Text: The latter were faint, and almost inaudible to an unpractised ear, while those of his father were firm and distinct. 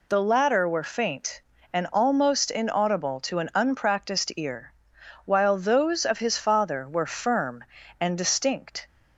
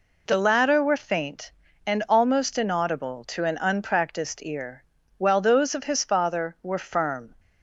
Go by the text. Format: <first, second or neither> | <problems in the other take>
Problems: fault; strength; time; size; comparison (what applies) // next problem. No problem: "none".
first | stops before "and distinct"; at 7.3 s